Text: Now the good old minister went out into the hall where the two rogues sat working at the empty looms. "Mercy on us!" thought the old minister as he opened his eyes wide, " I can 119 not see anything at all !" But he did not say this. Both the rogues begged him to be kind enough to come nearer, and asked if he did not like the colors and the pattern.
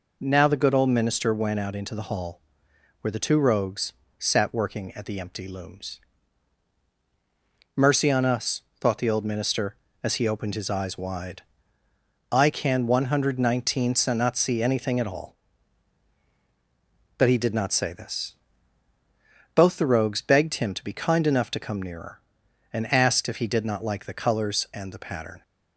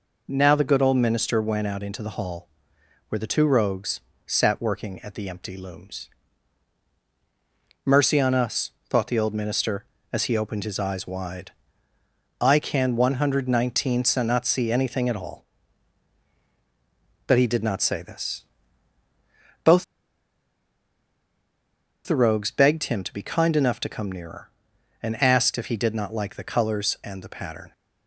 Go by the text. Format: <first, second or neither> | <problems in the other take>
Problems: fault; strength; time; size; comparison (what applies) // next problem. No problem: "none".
first | pauses between "hall" and "where"; noticeable; at 2.4 s; 0.62 s long; noticeable in the first // pauses between "rogues" and "sat"; slight; at 3.9 s; 0.26 s long; slight in the first // pauses between "Both" and "the"; strong; at 19.8 s; 2.2 s long